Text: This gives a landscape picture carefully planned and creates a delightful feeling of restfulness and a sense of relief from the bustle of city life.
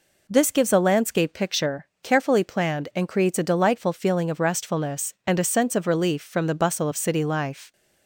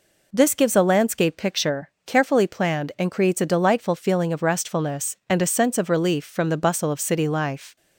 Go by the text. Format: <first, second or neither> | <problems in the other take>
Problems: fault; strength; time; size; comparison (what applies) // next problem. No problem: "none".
neither | pauses between "picture" and "carefully"; slight; the same in both